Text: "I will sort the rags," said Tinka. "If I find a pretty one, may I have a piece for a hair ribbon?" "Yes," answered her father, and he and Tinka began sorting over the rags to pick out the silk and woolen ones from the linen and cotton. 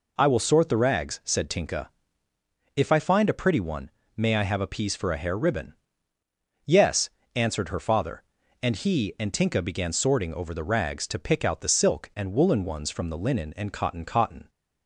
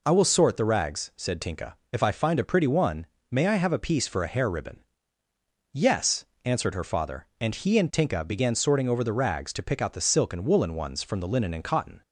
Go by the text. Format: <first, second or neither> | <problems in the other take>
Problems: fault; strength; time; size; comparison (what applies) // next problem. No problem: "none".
second | says "cotton" twice; at 14.0 s